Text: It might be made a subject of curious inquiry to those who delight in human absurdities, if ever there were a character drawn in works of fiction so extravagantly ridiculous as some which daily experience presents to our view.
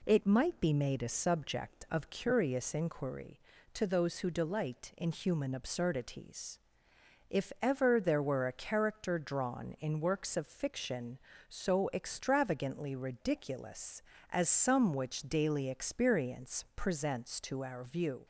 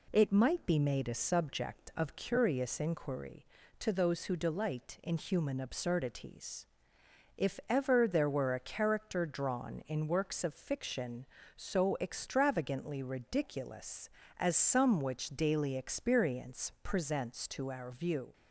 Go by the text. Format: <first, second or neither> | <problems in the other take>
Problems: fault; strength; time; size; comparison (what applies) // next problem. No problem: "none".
neither | none